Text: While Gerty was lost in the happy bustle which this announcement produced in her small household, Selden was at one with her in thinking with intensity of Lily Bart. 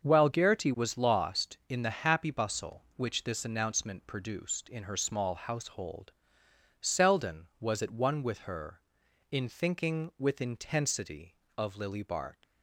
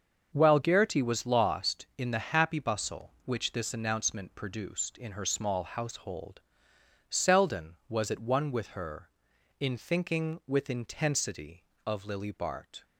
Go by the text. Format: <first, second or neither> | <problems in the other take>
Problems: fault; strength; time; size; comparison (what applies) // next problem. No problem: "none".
second | starts louder than the rest; until 1.0 s; 6.5 dB; also in the second // leaves "Bart" unfinished; at 12.4 s; 95 ms